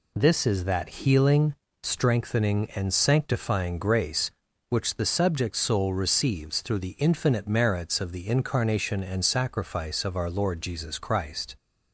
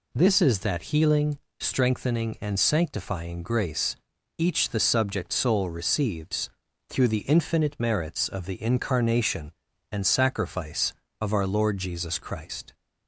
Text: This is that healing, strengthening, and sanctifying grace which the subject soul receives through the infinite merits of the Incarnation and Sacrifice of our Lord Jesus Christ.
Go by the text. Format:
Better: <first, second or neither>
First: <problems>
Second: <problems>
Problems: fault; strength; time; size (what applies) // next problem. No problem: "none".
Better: first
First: none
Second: says "each" for "which"; at 4.3 s // pauses between "receives" and "through"; at 6.4 s; 0.40 s long